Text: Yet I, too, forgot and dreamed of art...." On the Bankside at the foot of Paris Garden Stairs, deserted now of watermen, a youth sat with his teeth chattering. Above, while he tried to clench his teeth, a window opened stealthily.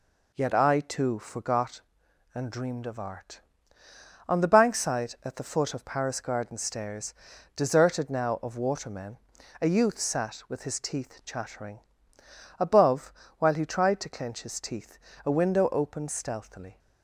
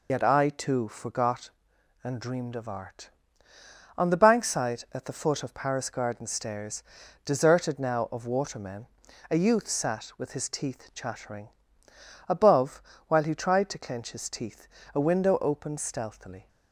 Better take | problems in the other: first | loses the start of "Yet"; at 0.0 s; 65 ms

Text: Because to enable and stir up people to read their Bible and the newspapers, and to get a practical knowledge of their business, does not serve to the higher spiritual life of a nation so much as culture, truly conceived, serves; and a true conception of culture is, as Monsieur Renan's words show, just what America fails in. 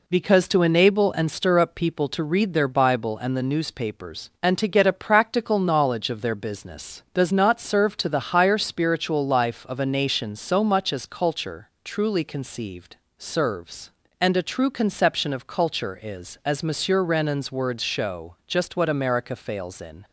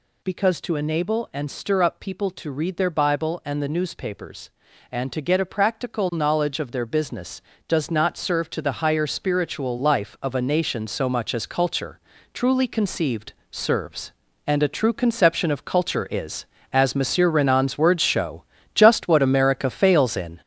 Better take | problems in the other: first | gets louder; throughout; 6.5 dB

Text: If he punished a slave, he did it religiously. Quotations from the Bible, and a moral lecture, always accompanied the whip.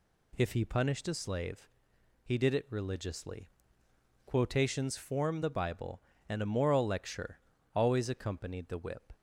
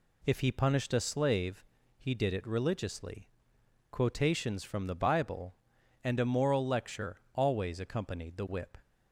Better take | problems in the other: second | says "form" for "from"; at 4.9 s

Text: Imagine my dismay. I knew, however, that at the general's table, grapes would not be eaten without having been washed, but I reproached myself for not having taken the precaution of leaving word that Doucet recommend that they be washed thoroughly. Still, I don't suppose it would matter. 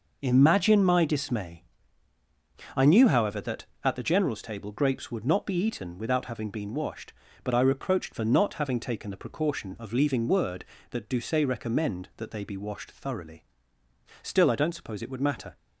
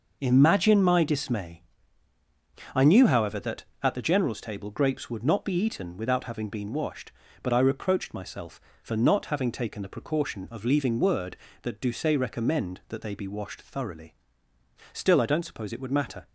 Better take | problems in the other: second | skips "myself"; at 8.1 s

